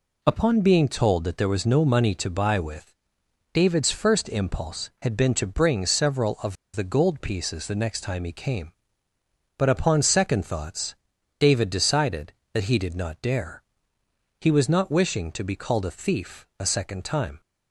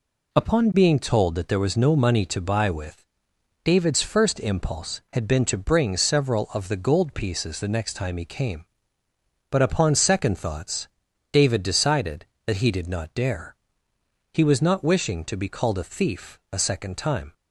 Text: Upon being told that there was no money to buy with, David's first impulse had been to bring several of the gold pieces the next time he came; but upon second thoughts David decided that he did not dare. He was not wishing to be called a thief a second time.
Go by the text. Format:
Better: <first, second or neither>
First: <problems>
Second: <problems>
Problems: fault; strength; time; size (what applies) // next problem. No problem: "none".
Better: second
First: pauses between "of" and "the"; slight; at 6.5 s; 0.20 s long // pauses between "thoughts" and "David"; noticeable; at 10.9 s; 0.46 s long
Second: pauses between "thoughts" and "David"; noticeable; at 10.8 s; 0.46 s long